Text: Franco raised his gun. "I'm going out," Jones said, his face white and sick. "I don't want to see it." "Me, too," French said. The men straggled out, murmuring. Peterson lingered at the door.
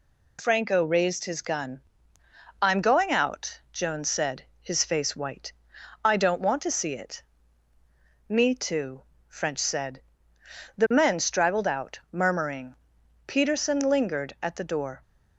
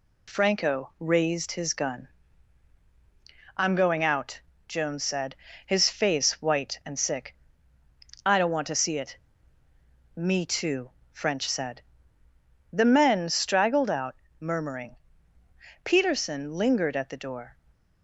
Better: second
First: skips "and sick"; at 5.7 s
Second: none

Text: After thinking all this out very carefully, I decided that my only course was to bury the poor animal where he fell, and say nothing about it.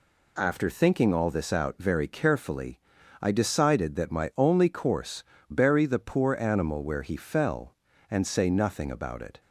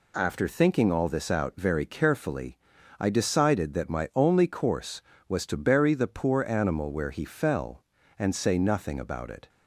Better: second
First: skips "was to"; at 5.3 s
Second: none

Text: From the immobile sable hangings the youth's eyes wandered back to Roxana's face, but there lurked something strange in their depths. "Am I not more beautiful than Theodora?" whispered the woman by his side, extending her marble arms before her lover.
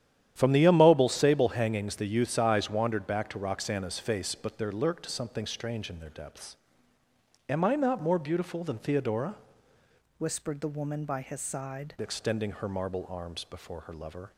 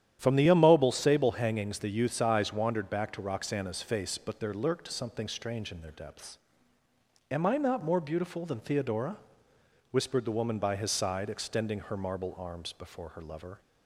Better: second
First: starts louder than the rest; strong; until 1.3 s; 10.5 dB // changes voice from "whispered" to "side"; from 10.1 to 11.9 s; 1.8 s long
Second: starts louder than the rest; strong; until 1.2 s; 10.5 dB

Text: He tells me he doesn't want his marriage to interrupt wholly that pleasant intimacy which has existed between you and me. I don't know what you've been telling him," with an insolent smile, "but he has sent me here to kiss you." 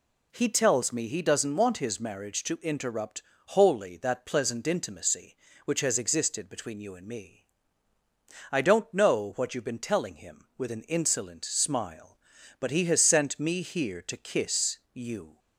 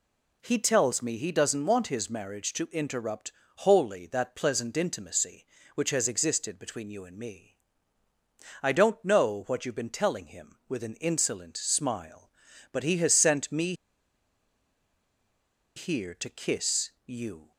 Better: first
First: pauses between "interrupt" and "wholly"; slight; at 3.2 s; 0.26 s long // pauses between "kiss" and "you"; slight; at 14.7 s; 0.16 s long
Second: pauses between "interrupt" and "wholly"; slight; at 3.3 s; 0.26 s long // pauses between "me" and "here"; strong; at 13.7 s; 2.0 s long // pauses between "kiss" and "you"; slight; at 16.8 s; 0.16 s long

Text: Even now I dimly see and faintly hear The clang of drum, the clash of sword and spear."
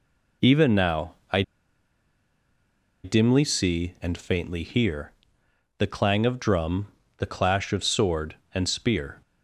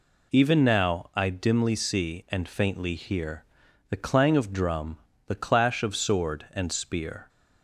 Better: second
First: pauses between "I" and "dimly"; strong; at 1.4 s; 1.6 s long // pauses between "hear" and "The"; noticeable; at 5.1 s; 0.68 s long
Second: pauses between "hear" and "The"; noticeable; at 3.4 s; 0.46 s long

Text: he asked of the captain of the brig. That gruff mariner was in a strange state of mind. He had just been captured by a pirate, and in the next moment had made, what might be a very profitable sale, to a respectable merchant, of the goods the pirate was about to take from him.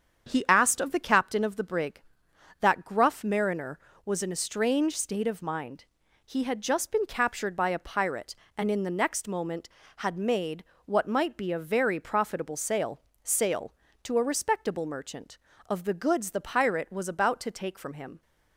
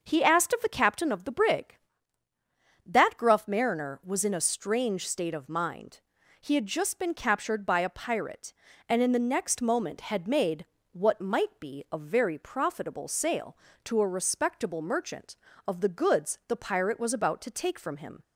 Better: second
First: starts louder than the rest; strong; until 1.3 s; 7.5 dB // says "sale" twice; at 13.2 s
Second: starts louder than the rest; noticeable; until 1.0 s; 6 dB

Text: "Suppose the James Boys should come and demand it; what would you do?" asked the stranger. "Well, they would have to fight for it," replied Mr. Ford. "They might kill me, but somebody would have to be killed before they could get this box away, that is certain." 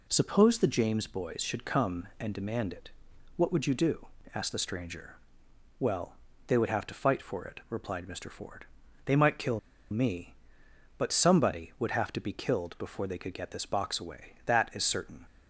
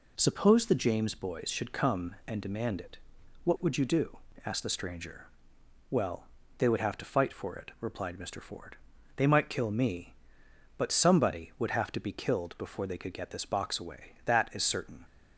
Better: second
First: pauses between "kill" and "me"; slight; at 9.5 s; 0.31 s long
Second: none

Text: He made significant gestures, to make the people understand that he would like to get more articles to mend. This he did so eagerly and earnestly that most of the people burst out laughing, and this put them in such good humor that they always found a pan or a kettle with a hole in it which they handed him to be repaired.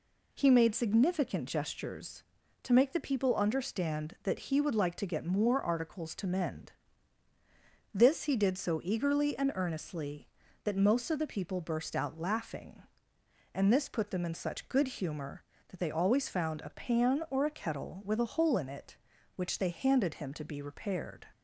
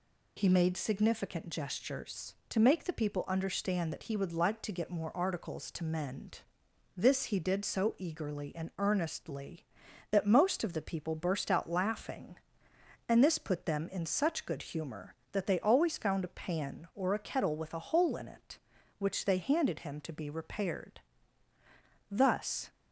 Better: first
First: none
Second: goes on to say "Thus"; from 22.1 s on; 0.58 s long

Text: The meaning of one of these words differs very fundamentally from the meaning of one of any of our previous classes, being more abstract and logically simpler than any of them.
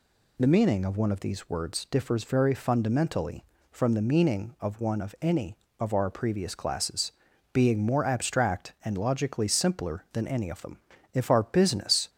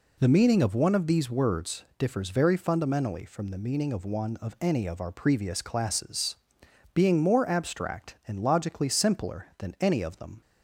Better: second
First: goes on to say "If our business"; noticeable; from 11.1 s on; 0.94 s long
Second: none

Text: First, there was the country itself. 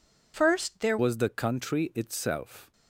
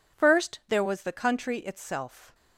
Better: second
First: changes voice at "was"; from 0.9 s on; 1.8 s long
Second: none

